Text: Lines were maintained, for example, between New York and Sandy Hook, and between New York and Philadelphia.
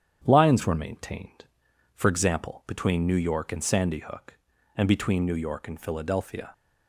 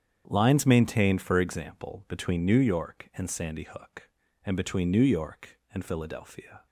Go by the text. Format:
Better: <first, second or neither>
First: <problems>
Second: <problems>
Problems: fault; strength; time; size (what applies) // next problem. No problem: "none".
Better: first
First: starts louder than the rest; strong; until 1.2 s; 9 dB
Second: starts louder than the rest; strong; until 1.2 s; 8.5 dB // skips "were"; at 0.6 s